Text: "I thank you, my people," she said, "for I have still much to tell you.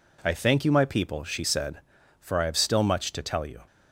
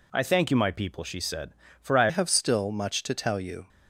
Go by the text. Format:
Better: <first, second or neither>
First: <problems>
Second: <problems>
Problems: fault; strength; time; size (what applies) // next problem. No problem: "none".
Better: first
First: none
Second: changes voice at "have"; from 2.0 s on; 1.6 s long